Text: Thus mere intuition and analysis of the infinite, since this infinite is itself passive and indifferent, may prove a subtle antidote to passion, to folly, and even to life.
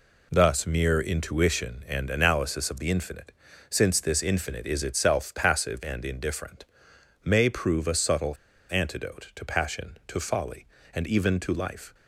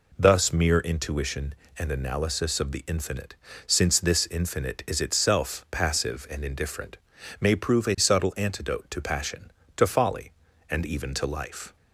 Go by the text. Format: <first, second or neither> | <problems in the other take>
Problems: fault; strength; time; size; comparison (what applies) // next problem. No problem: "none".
second | pauses between "subtle" and "antidote"; slight; at 8.3 s; 0.34 s long